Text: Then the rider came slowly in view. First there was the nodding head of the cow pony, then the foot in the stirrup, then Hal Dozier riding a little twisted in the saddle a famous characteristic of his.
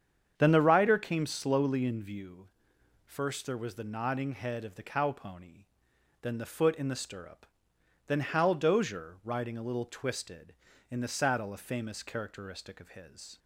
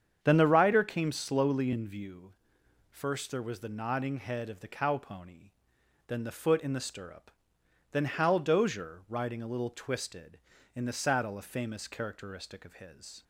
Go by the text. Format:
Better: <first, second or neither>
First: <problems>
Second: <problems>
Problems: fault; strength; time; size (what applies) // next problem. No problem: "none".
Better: neither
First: starts louder than the rest; strong; until 1.3 s; 8 dB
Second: starts louder than the rest; strong; until 1.2 s; 8 dB